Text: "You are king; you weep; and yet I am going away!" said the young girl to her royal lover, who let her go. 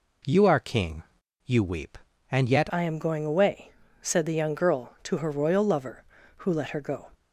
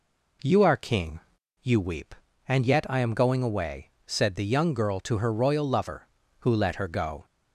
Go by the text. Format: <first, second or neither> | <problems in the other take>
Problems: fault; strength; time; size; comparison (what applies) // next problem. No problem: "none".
second | changes voice at "I"; from 2.7 s on; 4.3 s long